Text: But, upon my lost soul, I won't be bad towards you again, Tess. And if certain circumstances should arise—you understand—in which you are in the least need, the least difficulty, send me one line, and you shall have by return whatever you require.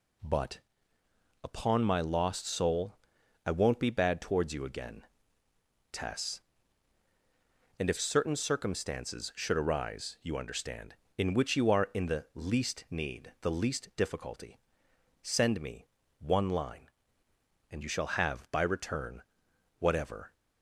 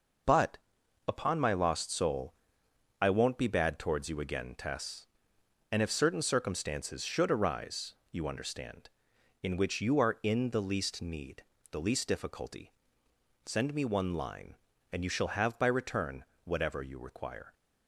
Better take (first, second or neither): second